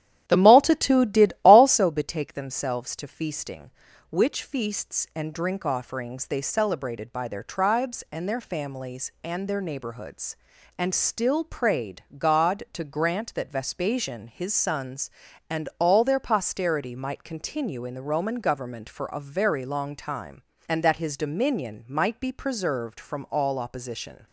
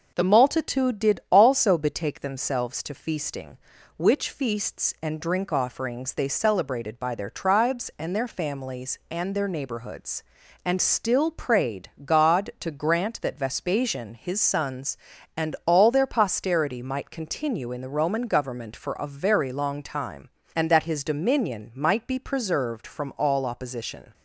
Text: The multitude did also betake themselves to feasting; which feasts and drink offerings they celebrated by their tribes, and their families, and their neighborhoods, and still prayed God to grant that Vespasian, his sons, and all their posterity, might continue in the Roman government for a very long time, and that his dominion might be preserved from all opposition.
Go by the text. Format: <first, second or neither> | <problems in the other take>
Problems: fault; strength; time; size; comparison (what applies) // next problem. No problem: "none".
second | starts louder than the rest; strong; until 1.8 s; 11 dB // pauses between "prayed" and "God"; slight; at 12.0 s; 0.16 s long; slight in the second